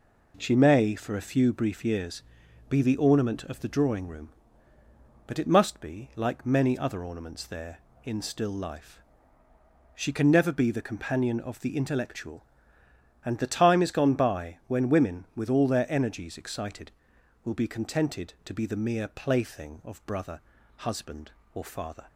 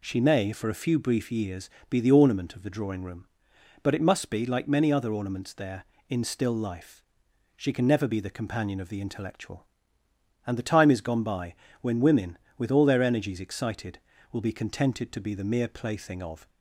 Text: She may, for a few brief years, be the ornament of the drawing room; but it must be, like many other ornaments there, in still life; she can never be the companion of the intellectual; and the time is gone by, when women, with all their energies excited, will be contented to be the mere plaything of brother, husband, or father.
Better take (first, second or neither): first